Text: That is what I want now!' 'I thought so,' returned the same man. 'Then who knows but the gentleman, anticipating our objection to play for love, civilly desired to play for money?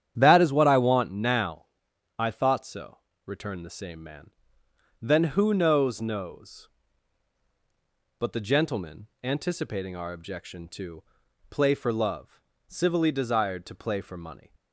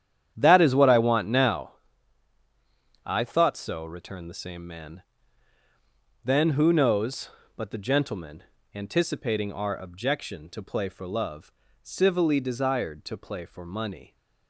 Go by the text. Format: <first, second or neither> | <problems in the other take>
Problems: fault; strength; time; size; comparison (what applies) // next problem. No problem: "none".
second | starts louder than the rest; strong; until 1.1 s; 9.5 dB; strong in the second // says "knows" twice; at 6.0 s // pauses between "to" and "play"; noticeable; at 11.0 s; 0.48 s long